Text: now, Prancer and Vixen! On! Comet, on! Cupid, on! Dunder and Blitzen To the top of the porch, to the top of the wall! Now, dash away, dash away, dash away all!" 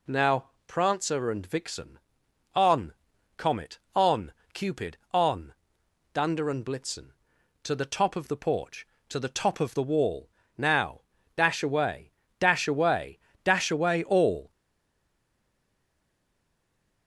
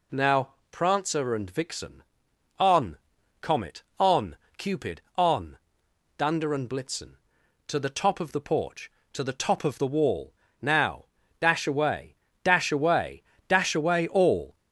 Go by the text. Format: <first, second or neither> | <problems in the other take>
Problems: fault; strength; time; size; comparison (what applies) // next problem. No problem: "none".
second | stays silent after the last word; strong; from 14.5 s on; 2.5 s long